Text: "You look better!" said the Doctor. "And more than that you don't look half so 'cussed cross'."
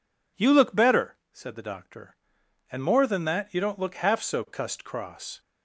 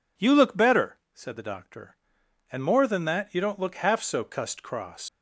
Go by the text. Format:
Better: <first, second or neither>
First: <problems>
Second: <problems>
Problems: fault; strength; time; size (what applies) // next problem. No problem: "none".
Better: first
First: none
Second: leaves "cross" unfinished; at 5.0 s; 100 ms